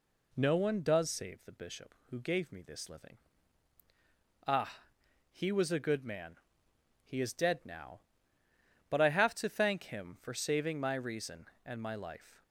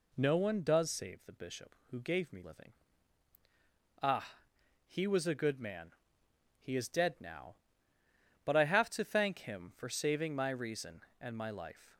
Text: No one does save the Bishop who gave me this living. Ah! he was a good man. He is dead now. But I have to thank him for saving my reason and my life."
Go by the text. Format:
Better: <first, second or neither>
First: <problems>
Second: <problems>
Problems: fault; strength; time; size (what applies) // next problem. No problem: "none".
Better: first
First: none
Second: skips "this"; at 2.4 s